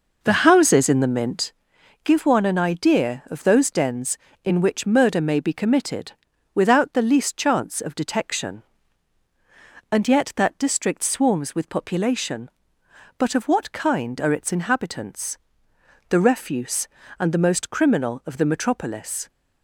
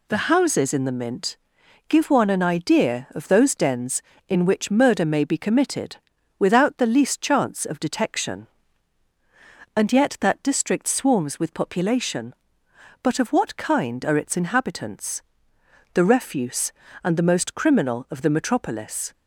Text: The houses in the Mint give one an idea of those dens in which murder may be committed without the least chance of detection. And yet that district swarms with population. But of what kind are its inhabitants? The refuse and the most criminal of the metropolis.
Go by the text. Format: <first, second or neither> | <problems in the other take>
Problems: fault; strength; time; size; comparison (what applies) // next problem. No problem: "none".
second | starts louder than the rest; noticeable; until 1.6 s; 5.5 dB // pauses between "Mint" and "give"; noticeable; at 1.5 s; 0.52 s long; noticeable in the second // pauses between "committed" and "without"; at 6.1 s; 0.40 s long; also in the second